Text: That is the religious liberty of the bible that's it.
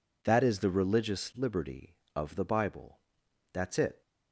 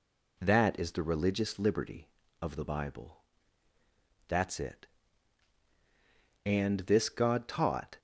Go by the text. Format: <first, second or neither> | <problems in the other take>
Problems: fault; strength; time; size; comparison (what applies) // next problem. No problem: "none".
first | pauses between "bible" and "that's"; at 3.1 s; 1.1 s long; noticeable in the first // goes on to say "And this god taught"; from 6.4 s on; 1.5 s long